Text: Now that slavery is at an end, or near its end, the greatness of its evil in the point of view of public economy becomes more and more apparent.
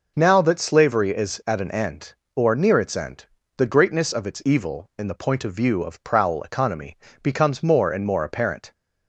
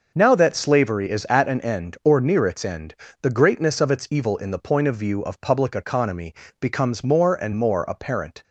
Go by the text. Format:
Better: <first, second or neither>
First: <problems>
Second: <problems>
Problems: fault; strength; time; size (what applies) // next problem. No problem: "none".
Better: second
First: says "prowl" for "public"; at 6.0 s // pauses between "economy" and "becomes"; slight; at 6.9 s; 0.26 s long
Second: pauses between "economy" and "becomes"; slight; at 6.3 s; 0.26 s long